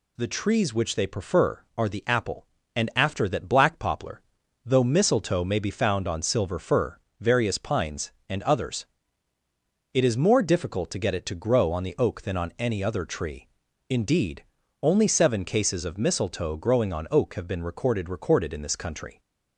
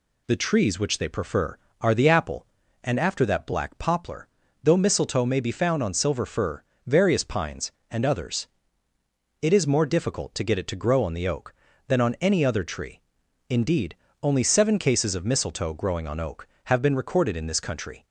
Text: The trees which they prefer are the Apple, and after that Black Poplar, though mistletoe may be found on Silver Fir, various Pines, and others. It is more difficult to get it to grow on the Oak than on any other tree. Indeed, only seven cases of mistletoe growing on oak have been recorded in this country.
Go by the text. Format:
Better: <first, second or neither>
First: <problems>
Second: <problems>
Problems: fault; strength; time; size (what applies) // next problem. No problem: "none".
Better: second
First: says "recorded" twice; at 18.0 s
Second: none